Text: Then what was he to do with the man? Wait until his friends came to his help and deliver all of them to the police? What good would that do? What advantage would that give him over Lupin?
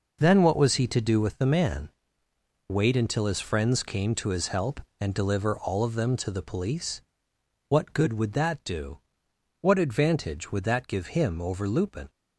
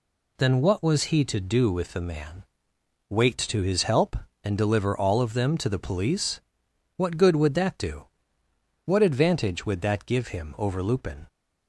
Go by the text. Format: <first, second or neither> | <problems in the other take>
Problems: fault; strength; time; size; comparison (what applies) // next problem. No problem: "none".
first | skips "until his friends came"; at 3.3 s